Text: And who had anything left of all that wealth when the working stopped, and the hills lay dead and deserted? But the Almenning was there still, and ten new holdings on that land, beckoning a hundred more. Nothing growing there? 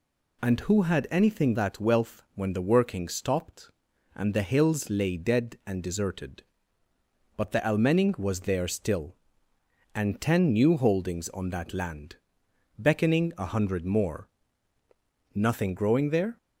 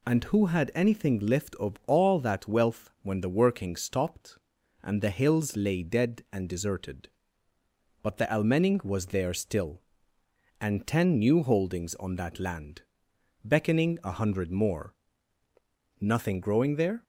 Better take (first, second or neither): second